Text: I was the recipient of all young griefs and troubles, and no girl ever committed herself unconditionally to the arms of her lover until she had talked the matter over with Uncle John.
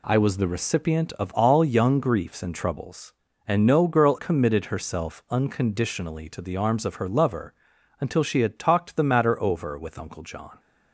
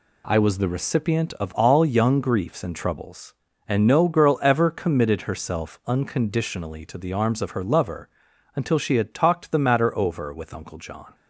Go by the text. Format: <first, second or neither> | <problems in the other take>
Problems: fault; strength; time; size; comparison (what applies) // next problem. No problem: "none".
second | skips "ever"; at 4.1 s // pauses between "lover" and "until"; noticeable; at 7.5 s; 0.46 s long; noticeable in the second